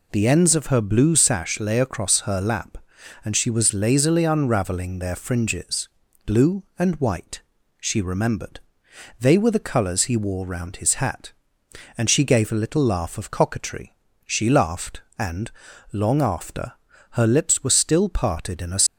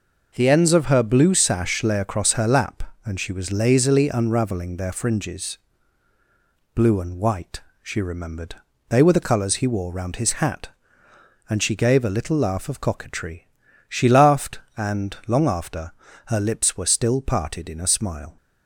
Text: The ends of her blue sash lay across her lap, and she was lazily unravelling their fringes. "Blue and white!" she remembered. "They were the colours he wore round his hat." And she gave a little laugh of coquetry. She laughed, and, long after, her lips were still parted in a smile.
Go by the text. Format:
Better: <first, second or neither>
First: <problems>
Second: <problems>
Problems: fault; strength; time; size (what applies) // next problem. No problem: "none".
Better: second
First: stops before "smile"; at 18.8 s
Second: none